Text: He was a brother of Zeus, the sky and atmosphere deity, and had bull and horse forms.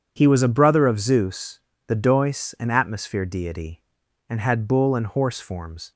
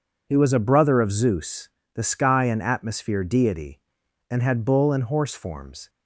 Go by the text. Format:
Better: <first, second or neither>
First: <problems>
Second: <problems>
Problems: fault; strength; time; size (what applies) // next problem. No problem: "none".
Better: second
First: starts louder than the rest; strong; until 1.1 s; 8 dB // says "dois" for "sky"; at 1.9 s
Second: none